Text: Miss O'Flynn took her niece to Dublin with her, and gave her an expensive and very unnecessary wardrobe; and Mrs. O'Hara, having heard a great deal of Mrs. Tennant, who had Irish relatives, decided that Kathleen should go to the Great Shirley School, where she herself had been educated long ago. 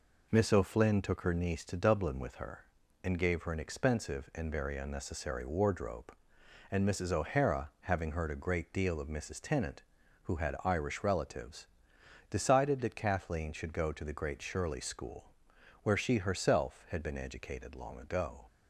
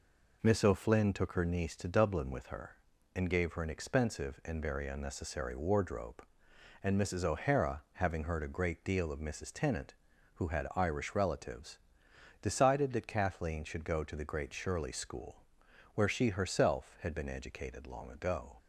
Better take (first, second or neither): neither